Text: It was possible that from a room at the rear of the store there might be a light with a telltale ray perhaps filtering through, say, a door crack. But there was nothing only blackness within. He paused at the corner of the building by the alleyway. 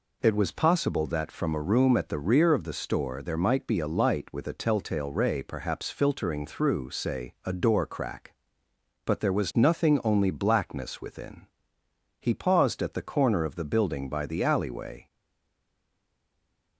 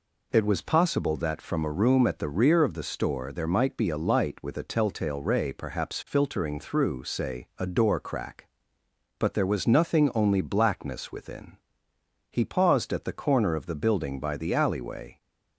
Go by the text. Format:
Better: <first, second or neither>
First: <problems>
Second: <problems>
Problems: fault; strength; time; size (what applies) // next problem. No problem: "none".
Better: second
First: stays silent after the last word; noticeable; from 15.0 s on; 1.7 s long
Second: none